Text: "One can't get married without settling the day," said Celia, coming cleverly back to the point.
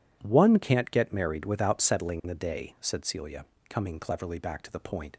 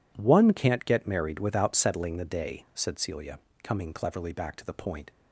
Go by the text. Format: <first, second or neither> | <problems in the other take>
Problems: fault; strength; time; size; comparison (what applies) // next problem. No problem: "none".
neither | none